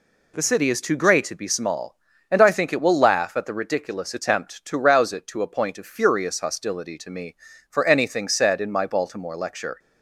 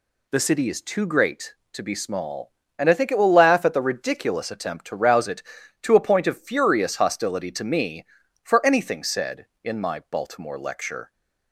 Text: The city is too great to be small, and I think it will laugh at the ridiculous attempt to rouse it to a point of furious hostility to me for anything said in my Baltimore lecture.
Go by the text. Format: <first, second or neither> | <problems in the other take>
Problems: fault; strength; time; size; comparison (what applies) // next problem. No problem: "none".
neither | none